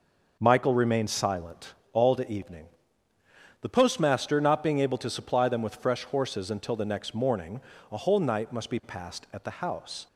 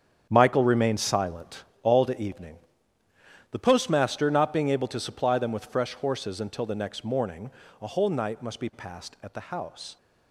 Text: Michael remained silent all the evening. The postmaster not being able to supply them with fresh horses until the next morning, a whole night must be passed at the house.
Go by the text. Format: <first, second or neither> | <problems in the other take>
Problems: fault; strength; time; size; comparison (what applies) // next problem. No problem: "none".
first | gets quieter; strong; throughout; 11.5 dB // pauses between "silent" and "all"; slight; at 1.6 s; 0.20 s long; slight in the first